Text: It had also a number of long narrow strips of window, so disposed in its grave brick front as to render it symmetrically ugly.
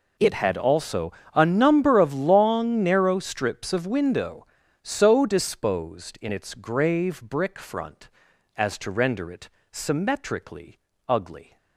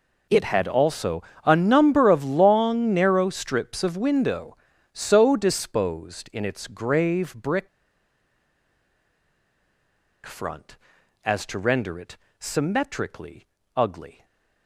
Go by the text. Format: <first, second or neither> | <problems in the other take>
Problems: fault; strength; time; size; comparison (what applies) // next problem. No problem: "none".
first | pauses between "also" and "a"; slight; at 1.2 s; 0.22 s long; slight in the first // pauses between "brick" and "front"; strong; at 7.6 s; 2.5 s long // pauses between "it" and "symmetrically"; slight; at 12.1 s; 0.22 s long; slight in the first // pauses between "symmetrically" and "ugly"; slight; at 13.4 s; 0.32 s long; slight in the first // stays silent after the last word; slight; from 14.1 s on; 0.5 s long